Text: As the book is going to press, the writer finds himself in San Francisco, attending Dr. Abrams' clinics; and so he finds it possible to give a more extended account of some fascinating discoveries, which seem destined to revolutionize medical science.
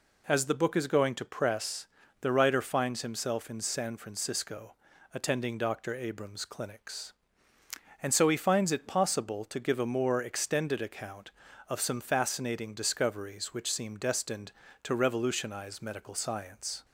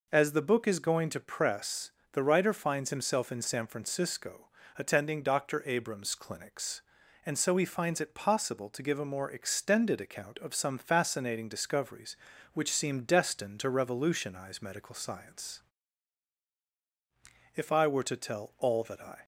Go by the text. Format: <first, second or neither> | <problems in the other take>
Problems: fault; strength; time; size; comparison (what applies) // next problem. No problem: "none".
first | goes on to say "If I were to tell all that I"; strong; from 17.5 s on; 1.7 s long